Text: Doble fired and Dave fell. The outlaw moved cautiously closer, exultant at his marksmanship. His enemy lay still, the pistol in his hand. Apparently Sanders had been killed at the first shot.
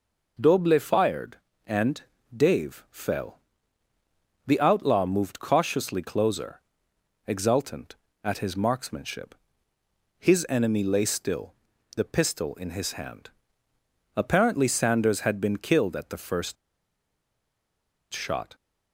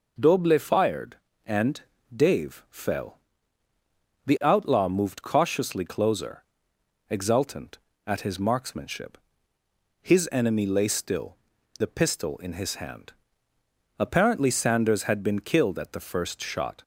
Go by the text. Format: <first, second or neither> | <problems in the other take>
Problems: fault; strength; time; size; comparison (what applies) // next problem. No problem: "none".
second | pauses between "and" and "Dave"; slight; at 2.0 s; 0.34 s long; slight in the second // pauses between "first" and "shot"; strong; at 16.5 s; 1.5 s long